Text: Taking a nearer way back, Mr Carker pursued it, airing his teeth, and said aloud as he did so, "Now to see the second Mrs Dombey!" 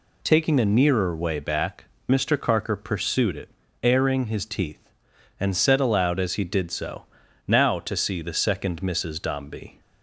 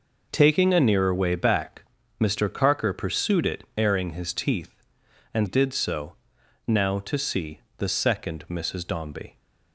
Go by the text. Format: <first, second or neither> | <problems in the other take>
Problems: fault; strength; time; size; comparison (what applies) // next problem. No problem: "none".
first | skips "said aloud as he"; at 5.4 s // pauses between "see" and "the"; slight; at 7.6 s; 0.16 s long